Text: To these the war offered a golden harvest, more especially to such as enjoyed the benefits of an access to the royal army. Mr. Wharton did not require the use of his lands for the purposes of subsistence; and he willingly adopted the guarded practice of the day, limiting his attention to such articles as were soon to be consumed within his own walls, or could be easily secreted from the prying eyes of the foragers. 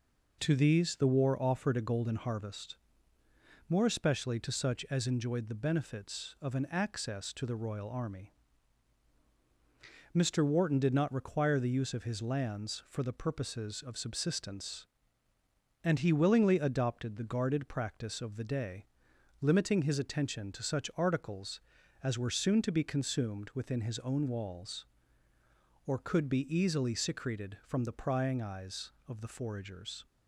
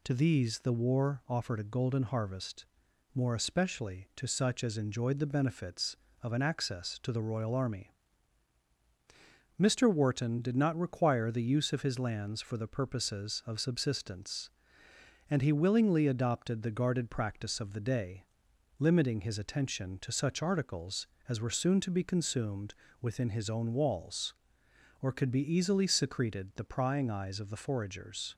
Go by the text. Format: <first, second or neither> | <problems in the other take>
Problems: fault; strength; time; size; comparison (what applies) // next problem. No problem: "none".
first | pauses between "consumed" and "within"; slight; at 22.7 s; 0.30 s long // skips "from"; at 26.5 s